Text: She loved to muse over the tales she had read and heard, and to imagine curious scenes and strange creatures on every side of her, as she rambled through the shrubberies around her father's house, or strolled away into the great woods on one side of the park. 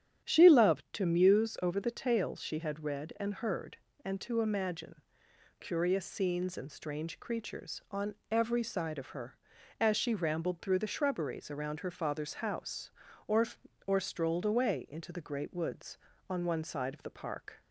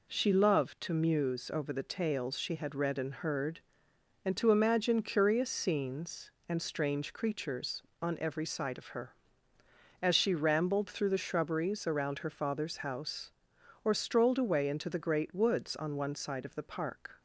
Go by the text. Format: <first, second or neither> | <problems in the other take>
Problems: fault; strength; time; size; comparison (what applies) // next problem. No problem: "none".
second | starts louder than the rest; strong; until 1.3 s; 9.5 dB // pauses between "imagine" and "curious"; noticeable; at 5.0 s; 0.58 s long // pauses between "on" and "every"; slight; at 8.1 s; 0.16 s long // says "or" twice; at 13.8 s